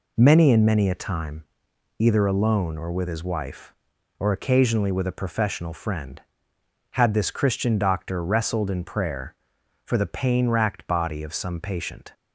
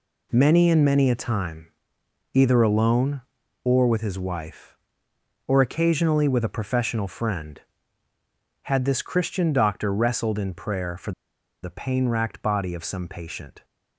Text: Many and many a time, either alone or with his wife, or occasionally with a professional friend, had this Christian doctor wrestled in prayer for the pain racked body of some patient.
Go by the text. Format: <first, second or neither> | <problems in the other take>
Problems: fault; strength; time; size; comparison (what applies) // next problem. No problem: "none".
first | pauses between "for" and "the"; noticeable; at 11.1 s; 0.51 s long